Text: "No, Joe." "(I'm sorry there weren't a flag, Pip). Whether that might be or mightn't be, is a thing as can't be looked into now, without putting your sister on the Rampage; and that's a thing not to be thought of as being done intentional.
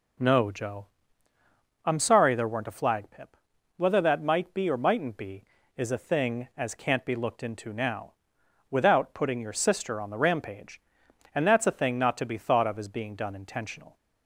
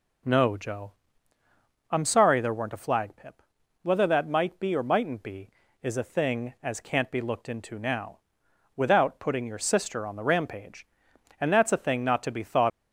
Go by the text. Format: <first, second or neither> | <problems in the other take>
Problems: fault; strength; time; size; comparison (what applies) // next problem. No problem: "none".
first | stops before "of as being done intentional"; at 12.7 s